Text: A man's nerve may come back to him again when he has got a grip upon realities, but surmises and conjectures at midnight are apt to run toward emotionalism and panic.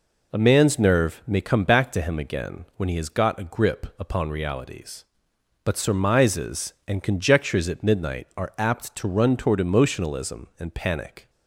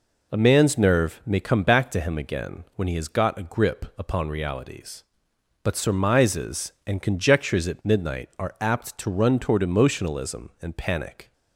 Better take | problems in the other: neither | none

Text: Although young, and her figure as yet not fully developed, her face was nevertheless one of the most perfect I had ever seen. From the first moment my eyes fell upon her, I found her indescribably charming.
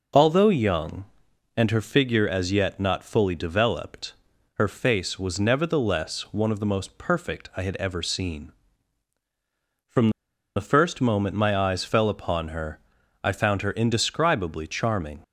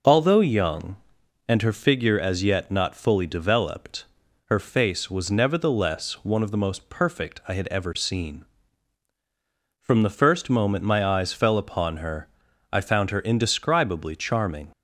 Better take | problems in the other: second | pauses between "From" and "the"; at 10.1 s; 0.45 s long

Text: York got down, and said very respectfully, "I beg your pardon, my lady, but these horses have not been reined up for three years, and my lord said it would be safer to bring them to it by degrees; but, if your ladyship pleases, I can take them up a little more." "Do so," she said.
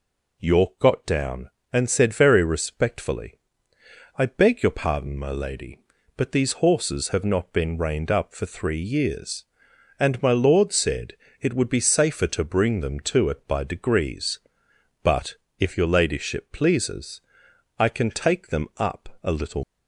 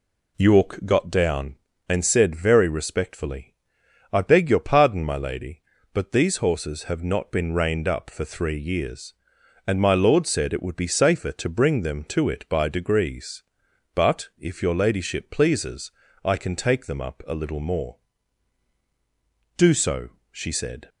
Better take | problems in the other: second | pauses between "said" and "it"; slight; at 11.1 s; 0.26 s long // stops before "more Do so she said"; at 19.6 s

